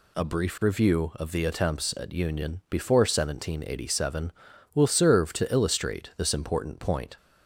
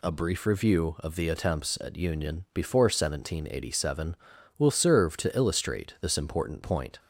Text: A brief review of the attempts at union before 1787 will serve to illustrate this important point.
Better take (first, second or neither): neither